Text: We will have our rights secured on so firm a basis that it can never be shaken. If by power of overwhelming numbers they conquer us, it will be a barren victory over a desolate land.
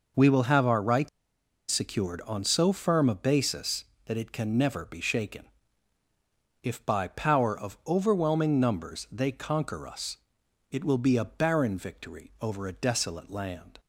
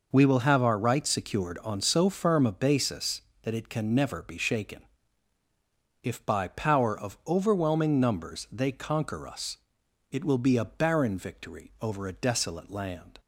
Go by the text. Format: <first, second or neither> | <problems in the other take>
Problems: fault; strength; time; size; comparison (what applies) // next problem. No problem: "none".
second | pauses between "rights" and "secured"; noticeable; at 1.0 s; 0.61 s long